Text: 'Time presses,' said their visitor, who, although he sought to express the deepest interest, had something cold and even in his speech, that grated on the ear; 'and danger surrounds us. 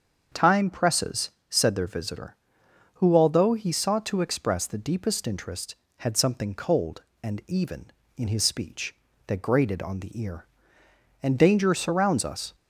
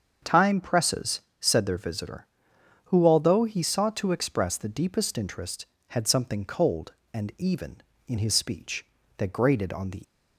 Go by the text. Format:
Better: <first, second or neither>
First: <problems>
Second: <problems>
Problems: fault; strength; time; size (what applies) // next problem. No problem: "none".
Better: first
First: starts louder than the rest; until 1.5 s; 7 dB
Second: starts louder than the rest; until 1.4 s; 7 dB // stops before "ear and danger surrounds us"; at 10.0 s